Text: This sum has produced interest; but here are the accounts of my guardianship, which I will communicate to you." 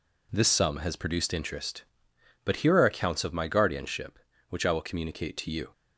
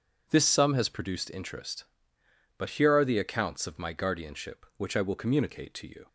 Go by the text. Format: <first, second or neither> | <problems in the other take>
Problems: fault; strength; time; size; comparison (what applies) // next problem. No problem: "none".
second | skips "the"; at 2.8 s